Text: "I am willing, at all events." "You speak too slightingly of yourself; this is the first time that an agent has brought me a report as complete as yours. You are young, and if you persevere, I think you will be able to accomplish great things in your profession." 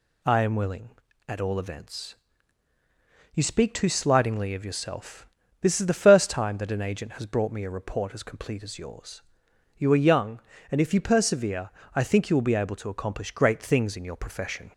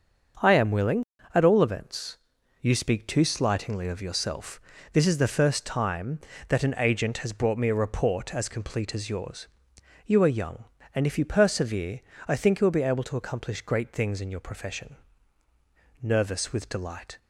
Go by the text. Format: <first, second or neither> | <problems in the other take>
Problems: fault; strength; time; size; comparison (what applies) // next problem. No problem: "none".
first | starts louder than the rest; until 1.7 s; 6.5 dB // goes on to say "Nervous with delight"; noticeable; from 16.0 s on; 1.1 s long